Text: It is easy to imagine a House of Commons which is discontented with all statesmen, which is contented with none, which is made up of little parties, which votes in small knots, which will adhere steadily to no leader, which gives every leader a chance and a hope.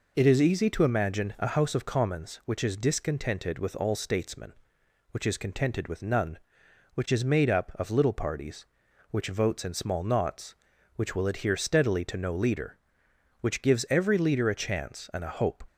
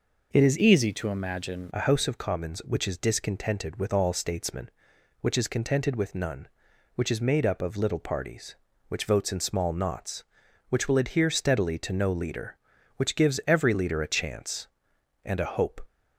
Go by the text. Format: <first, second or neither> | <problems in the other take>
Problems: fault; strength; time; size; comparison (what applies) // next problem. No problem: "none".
first | changes voice from "easy" to "imagine"; from 0.5 to 1.7 s; 1.2 s long